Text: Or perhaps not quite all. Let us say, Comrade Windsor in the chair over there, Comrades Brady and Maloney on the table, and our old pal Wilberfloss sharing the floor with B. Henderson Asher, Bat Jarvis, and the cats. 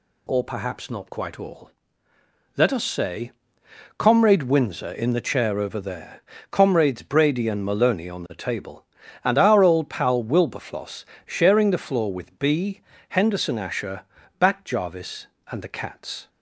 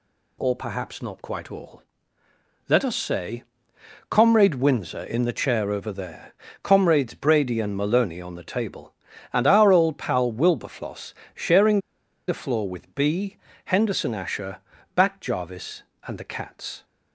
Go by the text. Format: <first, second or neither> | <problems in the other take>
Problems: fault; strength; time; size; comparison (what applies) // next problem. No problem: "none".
first | pauses between "Wilberfloss" and "sharing"; slight; at 11.1 s; 0.22 s long; slight in the first // pauses between "sharing" and "the"; noticeable; at 11.7 s; 0.48 s long